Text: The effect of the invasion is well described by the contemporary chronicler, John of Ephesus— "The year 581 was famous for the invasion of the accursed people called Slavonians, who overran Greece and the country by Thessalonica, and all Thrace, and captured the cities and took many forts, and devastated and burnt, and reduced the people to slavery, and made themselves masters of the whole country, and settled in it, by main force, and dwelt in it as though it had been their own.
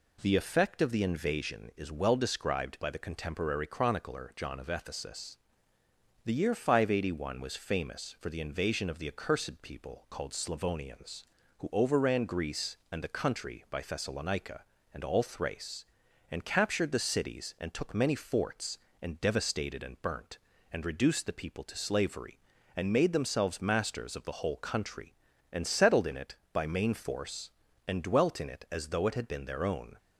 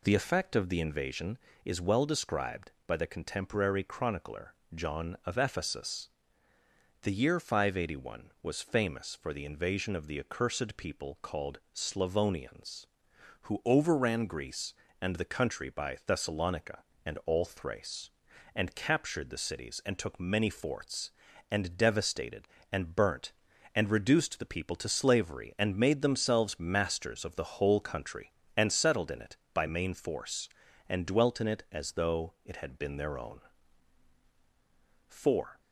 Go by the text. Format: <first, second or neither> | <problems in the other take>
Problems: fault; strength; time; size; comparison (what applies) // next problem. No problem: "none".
first | goes on to say "Four"; from 35.0 s on; 0.52 s long